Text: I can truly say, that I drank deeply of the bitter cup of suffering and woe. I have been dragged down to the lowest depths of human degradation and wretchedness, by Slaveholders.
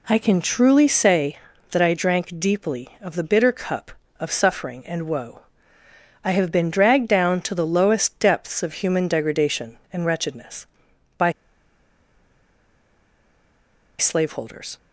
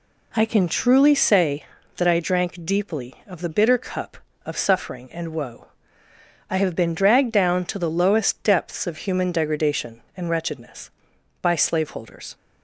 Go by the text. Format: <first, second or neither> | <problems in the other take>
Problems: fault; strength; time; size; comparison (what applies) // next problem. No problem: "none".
second | pauses between "by" and "Slaveholders"; strong; at 11.3 s; 2.6 s long